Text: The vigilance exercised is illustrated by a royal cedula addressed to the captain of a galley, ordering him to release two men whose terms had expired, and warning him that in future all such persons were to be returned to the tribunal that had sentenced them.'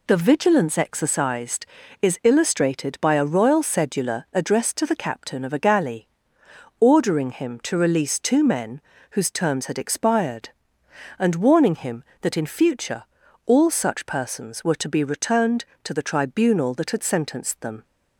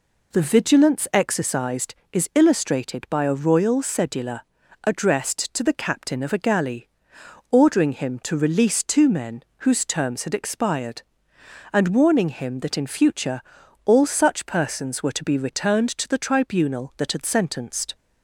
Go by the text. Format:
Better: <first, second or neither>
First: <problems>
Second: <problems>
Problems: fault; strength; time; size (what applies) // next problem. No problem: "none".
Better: first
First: pauses between "men" and "whose"; slight; at 8.7 s; 0.32 s long // pauses between "future" and "all"; at 13.0 s; 0.42 s long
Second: pauses between "cedula" and "addressed"; at 4.4 s; 0.42 s long // pauses between "men" and "whose"; slight; at 9.4 s; 0.22 s long // pauses between "future" and "all"; at 13.4 s; 0.44 s long // stops before "them"; at 17.9 s